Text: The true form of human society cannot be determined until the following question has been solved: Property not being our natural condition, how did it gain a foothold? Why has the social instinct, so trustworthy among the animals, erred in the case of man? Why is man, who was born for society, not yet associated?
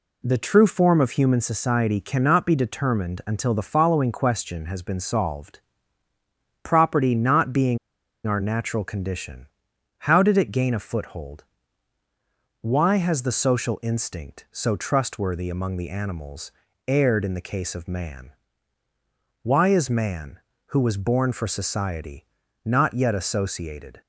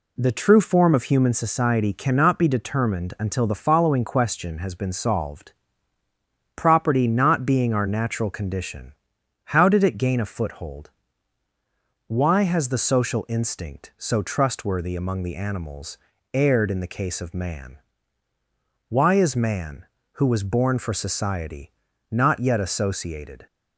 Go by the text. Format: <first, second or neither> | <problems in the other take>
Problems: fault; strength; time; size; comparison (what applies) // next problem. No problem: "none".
second | pauses between "being" and "our"; noticeable; at 7.7 s; 0.48 s long